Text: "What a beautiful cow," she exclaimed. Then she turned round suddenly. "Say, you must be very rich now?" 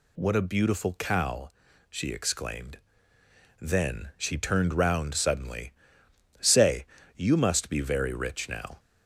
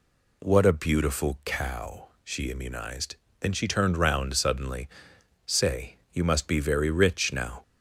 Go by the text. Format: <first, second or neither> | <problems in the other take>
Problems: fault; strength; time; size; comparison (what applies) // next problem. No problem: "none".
first | says "immunized" for "exclaimed"; at 2.4 s